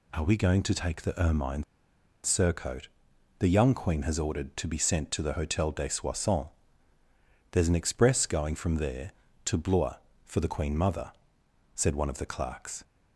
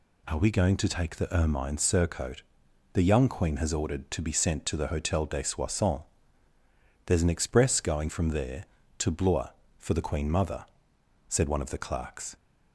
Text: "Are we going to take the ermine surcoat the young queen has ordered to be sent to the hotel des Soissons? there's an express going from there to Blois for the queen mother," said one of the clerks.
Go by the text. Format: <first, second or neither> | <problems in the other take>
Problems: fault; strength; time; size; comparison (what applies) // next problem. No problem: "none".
second | pauses between "ermine" and "surcoat"; noticeable; at 1.6 s; 0.60 s long // pauses between "surcoat" and "the"; noticeable; at 2.8 s; 0.50 s long; noticeable in the second